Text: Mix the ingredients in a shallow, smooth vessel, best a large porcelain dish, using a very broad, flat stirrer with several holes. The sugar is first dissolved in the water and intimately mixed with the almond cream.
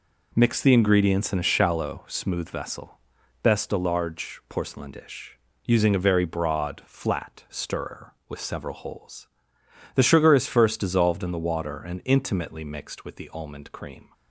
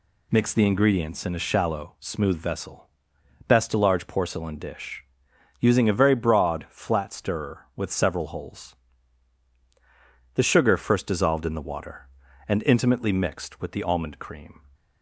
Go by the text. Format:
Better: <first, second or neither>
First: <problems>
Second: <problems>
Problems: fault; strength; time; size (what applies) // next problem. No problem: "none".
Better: first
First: none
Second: skips "is"; at 10.7 s